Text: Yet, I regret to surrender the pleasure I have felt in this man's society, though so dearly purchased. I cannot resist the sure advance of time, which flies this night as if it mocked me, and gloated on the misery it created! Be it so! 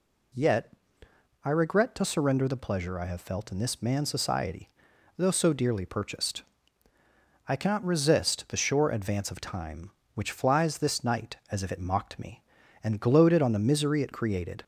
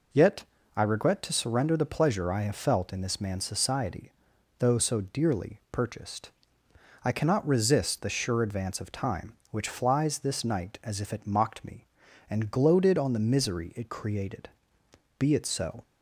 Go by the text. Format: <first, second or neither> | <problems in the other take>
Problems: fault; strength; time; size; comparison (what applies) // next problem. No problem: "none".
second | stops before "Be it so"; at 14.6 s